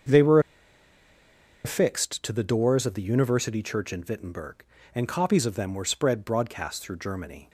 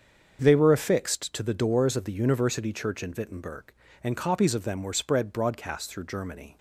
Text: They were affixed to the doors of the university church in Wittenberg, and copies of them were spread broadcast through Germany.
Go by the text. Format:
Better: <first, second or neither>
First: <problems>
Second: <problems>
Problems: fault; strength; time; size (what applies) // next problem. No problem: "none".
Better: second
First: starts louder than the rest; until 2.3 s; 6.5 dB // pauses between "were" and "affixed"; strong; at 0.3 s; 1.2 s long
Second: starts louder than the rest; until 1.4 s; 7 dB